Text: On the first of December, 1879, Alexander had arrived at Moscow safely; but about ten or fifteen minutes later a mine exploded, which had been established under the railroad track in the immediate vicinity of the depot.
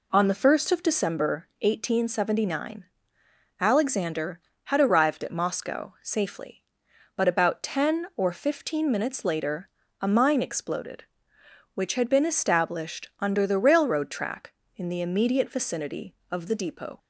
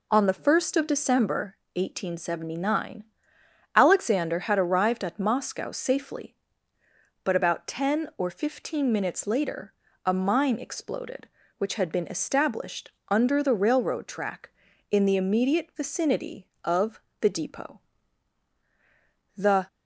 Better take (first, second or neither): first